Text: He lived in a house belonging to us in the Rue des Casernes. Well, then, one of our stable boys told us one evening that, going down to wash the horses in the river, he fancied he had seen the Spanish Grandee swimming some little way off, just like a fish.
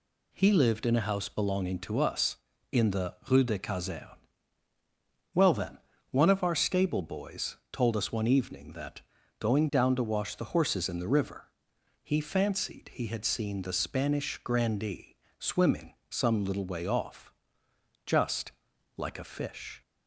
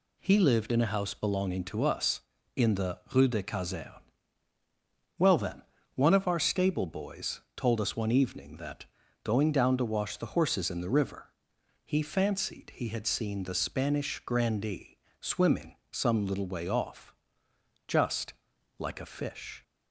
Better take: neither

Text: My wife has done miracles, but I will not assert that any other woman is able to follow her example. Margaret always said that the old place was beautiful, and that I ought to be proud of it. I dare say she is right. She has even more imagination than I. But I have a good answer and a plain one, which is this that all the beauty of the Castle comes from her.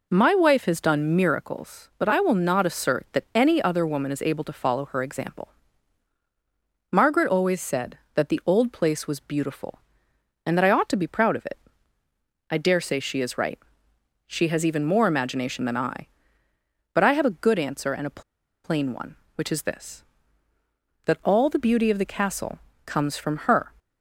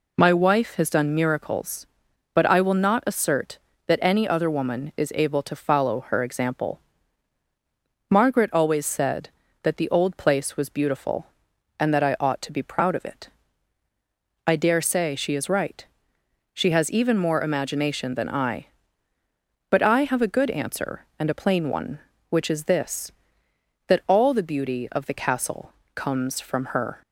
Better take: second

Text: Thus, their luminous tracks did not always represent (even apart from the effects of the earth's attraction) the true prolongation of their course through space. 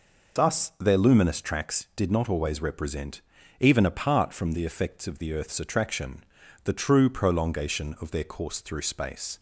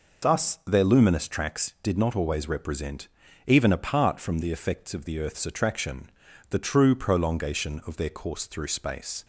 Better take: neither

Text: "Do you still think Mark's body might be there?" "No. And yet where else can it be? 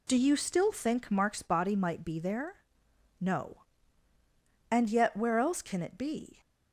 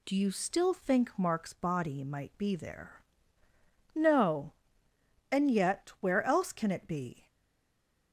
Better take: first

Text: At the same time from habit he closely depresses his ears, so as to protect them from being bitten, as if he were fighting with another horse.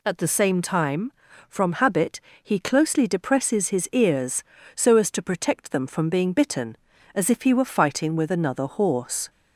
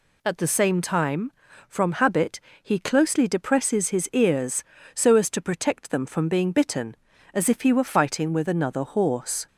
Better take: neither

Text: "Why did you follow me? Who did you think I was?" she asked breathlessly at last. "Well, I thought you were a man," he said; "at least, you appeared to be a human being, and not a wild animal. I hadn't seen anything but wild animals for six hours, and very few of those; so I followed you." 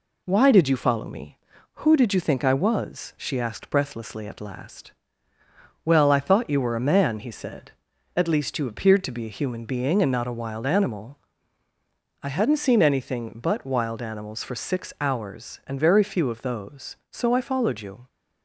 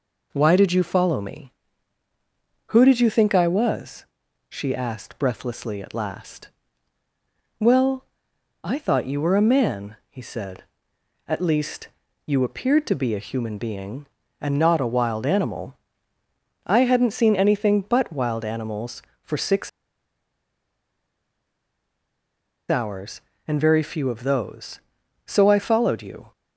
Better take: first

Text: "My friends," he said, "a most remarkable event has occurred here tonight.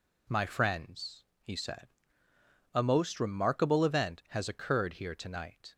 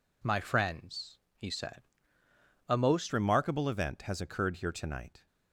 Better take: first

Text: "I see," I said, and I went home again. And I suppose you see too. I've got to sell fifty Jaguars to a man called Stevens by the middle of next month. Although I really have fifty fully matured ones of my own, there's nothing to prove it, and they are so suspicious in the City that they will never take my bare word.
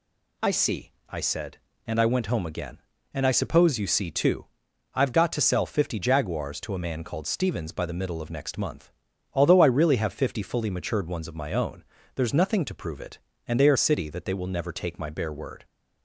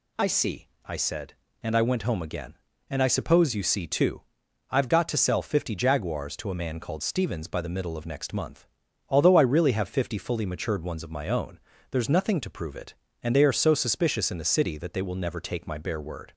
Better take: second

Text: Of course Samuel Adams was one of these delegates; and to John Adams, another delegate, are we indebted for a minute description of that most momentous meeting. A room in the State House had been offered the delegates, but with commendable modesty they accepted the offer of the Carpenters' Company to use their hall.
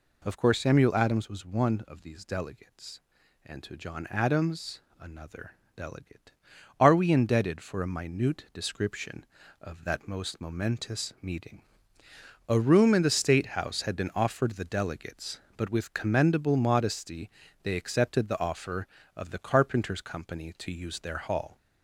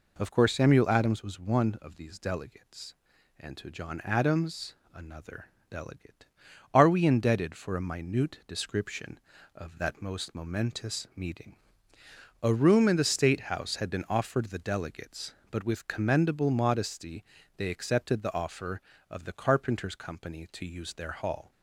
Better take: second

